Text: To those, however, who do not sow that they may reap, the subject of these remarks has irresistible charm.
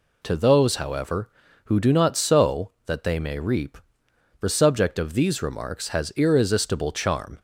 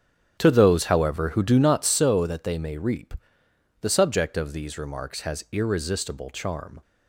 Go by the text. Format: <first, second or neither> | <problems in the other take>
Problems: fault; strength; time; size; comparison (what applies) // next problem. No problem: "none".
first | starts louder than the rest; strong; until 2.1 s; 9.5 dB